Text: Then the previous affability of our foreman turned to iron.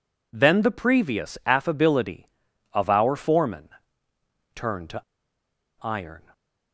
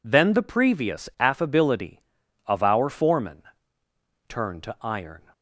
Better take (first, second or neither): second